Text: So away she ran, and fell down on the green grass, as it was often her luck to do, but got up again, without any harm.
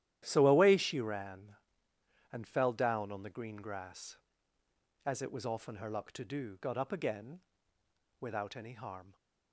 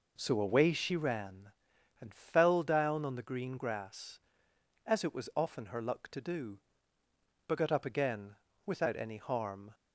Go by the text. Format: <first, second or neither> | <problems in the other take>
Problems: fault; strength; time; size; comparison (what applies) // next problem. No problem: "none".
second | starts louder than the rest; strong; until 1.2 s; 12 dB // skips "but"; at 6.6 s